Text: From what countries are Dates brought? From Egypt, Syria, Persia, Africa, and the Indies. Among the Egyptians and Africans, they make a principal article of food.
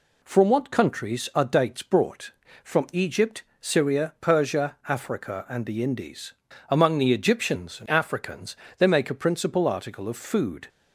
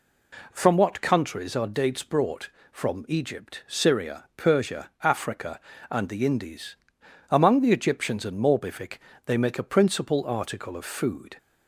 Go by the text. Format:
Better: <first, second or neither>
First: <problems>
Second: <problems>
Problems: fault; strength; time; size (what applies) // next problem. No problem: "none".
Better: first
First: none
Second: says "Morbific" for "Africans"; at 8.3 s